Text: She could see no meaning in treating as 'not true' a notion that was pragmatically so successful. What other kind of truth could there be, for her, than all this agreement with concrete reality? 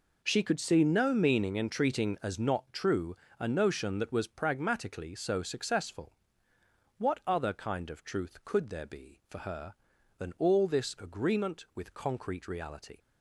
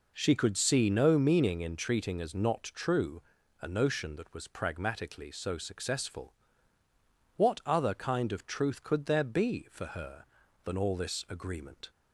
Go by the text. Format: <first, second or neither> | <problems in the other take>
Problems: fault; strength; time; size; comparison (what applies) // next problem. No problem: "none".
first | pauses between "true" and "a"; at 3.1 s; 0.40 s long; slight in the first // stops before "with concrete reality"; at 11.8 s